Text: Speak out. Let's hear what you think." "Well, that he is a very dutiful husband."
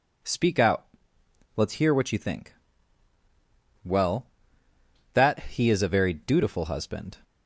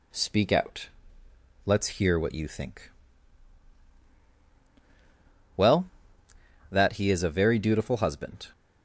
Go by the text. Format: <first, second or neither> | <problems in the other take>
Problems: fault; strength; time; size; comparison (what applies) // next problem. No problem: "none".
neither | none